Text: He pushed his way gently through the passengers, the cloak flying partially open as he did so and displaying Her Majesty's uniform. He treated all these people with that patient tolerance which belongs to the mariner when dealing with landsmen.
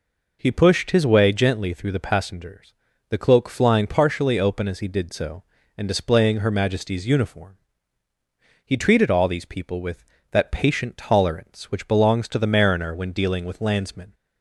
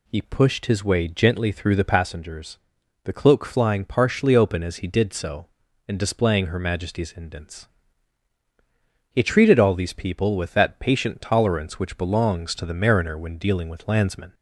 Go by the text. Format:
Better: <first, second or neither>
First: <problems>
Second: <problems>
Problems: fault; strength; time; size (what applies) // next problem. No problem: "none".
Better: first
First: none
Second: says "indents" for "uniform"; at 7.1 s